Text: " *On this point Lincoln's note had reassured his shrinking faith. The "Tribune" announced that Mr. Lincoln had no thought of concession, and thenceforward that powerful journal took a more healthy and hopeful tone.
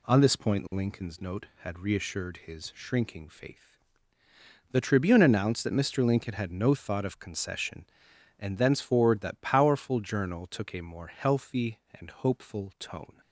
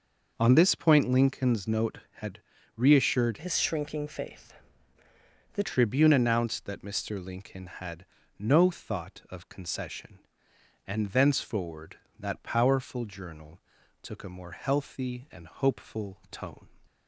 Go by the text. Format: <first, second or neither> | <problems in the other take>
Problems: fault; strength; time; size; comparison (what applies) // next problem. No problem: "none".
first | pauses between "had" and "reassured"; slight; at 2.4 s; 0.34 s long // changes voice from "his" to "The"; from 3.4 to 5.6 s; 2.2 s long // pauses between "had" and "no"; slight; at 8.0 s; 0.36 s long // pauses between "journal" and "took"; at 13.5 s; 0.42 s long